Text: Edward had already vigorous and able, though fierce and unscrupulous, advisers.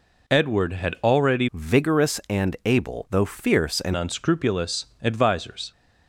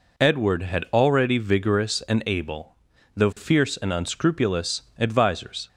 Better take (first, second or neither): second